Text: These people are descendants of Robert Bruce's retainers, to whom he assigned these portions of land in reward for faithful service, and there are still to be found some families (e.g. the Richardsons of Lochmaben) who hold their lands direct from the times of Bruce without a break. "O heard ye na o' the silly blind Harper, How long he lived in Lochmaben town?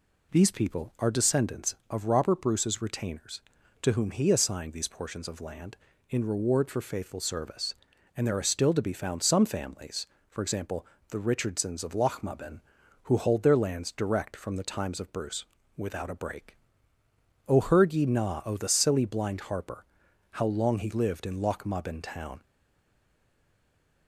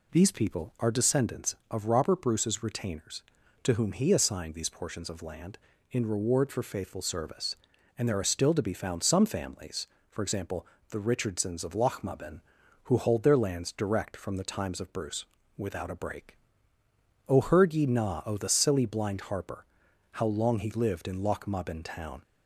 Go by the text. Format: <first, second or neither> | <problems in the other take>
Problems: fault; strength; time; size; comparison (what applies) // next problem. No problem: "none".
second | pauses between "Bruce" and "without"; slight; at 15.4 s; 0.32 s long; slight in the second // stays silent after the last word; noticeable; from 22.4 s on; 1.6 s long